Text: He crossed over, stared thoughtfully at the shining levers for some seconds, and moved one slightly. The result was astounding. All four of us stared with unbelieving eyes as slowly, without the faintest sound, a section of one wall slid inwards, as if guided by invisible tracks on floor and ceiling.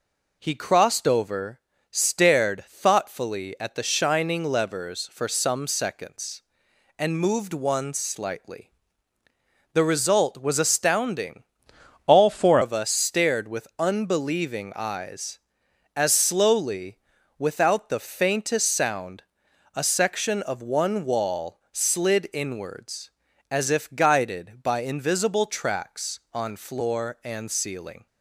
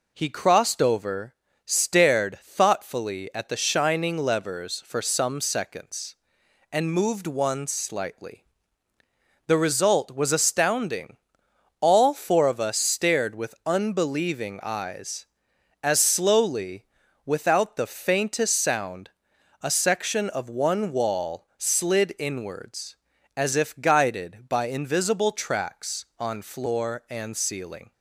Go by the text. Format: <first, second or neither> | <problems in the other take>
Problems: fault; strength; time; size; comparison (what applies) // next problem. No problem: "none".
second | changes voice from "All" to "four"; from 12.0 to 12.5 s; 0.5 s long